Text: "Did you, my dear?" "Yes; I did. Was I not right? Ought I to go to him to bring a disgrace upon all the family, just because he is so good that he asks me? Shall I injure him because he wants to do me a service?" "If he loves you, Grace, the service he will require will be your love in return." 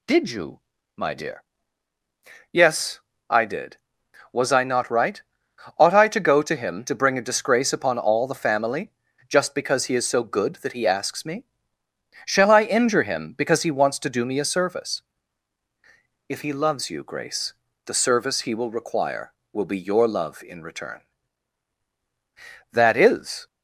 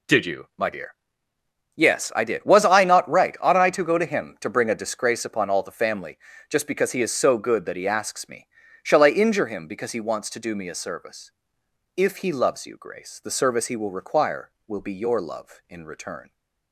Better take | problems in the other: second | goes on to say "That is"; noticeable; from 22.7 s on; 0.74 s long

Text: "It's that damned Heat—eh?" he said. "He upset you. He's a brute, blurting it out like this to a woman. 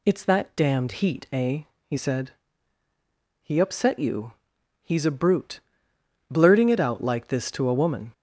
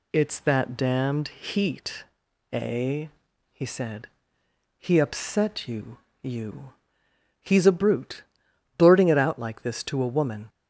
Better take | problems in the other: first | says "you" twice; at 6.2 s

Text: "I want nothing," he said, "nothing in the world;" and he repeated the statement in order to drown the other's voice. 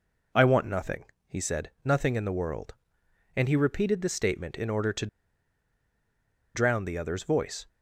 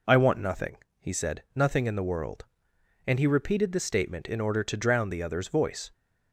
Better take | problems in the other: second | pauses between "to" and "drown"; strong; at 5.0 s; 1.4 s long

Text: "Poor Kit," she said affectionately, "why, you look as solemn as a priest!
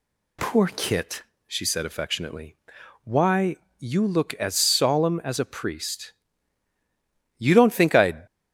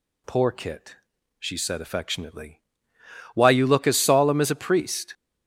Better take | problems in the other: second | goes on to say "You don't think I'd"; noticeable; from 7.3 s on; 0.88 s long

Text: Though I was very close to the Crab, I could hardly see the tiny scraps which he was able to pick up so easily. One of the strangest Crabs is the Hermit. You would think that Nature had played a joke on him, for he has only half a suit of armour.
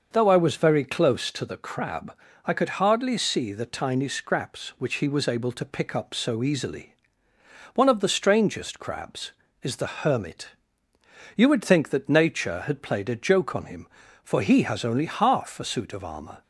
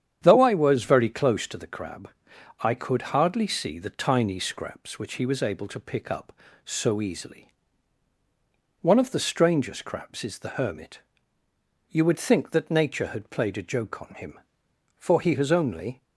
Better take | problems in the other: first | starts louder than the rest; strong; until 1.2 s; 9 dB; noticeable in the first // stops before "half a suit of armour"; at 16.0 s

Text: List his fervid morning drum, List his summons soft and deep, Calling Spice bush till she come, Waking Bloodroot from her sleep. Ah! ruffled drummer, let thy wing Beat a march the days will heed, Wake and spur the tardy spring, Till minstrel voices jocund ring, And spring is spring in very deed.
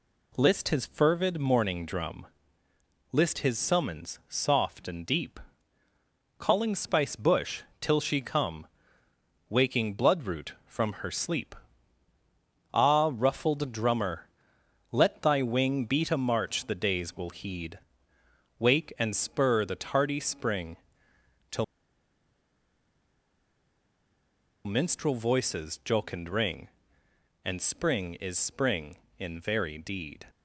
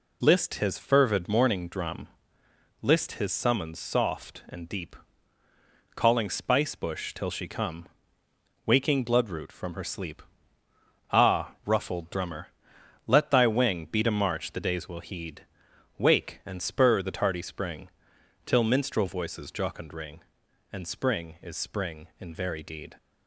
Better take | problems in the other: second | pauses between "bush" and "till"; slight; at 7.6 s; 0.18 s long // pauses between "Till" and "minstrel"; strong; at 21.6 s; 3.0 s long

